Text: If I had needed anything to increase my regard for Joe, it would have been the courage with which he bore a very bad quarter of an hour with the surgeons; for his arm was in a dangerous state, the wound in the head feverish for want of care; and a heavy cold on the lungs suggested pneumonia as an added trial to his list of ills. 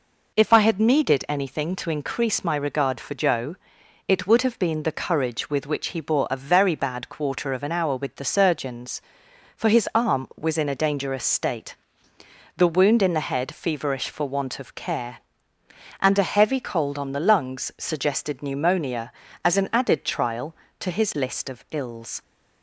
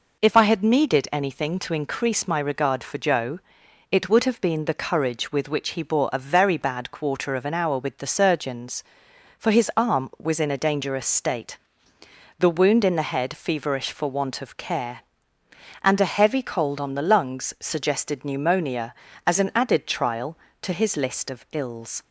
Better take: neither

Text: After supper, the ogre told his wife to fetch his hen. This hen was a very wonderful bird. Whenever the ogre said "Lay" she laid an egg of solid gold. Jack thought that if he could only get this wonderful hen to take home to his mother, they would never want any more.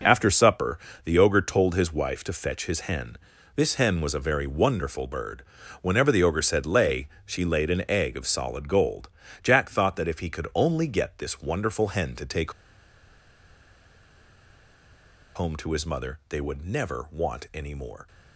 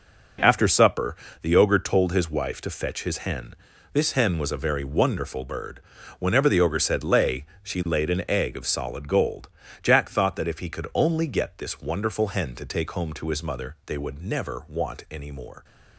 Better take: second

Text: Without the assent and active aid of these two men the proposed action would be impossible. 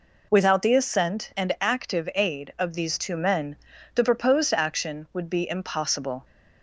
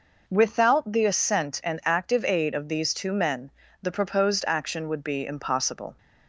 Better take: neither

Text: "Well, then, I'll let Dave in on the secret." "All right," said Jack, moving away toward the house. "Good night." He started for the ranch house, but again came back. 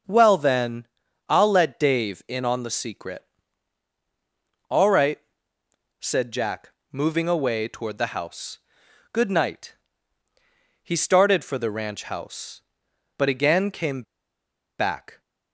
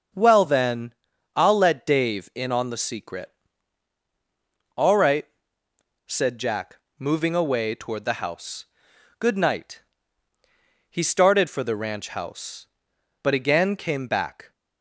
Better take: second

